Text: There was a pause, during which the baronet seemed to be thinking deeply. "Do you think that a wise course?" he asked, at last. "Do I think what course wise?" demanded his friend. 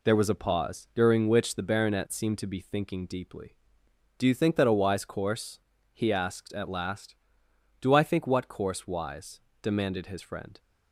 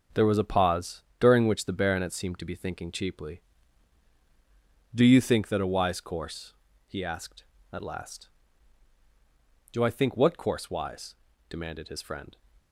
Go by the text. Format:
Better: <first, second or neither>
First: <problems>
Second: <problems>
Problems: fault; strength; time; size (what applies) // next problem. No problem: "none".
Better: first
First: none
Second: starts louder than the rest; until 1.3 s; 6.5 dB // says "cheaply" for "deeply"; at 2.9 s